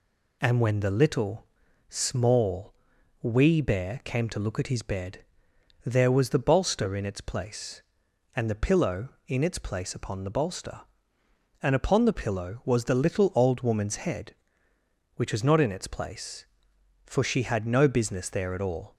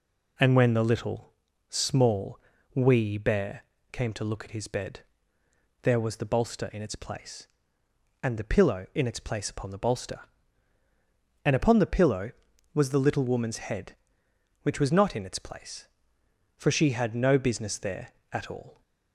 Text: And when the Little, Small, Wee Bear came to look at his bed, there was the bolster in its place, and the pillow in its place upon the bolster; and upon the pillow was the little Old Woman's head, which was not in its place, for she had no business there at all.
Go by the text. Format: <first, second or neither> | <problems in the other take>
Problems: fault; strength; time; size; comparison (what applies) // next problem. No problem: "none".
first | pauses between "Bear" and "came"; slight; at 3.6 s; 0.30 s long // skips "Old"; at 13.2 s